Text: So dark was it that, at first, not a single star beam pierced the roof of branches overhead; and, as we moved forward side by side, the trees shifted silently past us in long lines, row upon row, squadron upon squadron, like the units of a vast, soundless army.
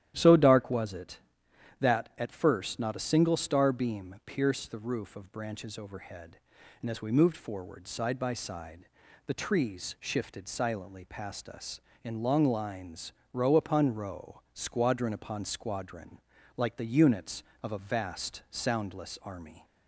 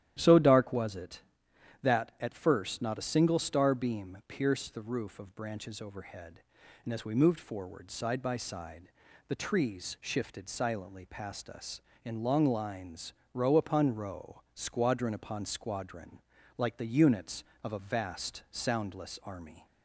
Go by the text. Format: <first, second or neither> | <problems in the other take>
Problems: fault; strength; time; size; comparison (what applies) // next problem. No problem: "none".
neither | starts louder than the rest; strong; the same in both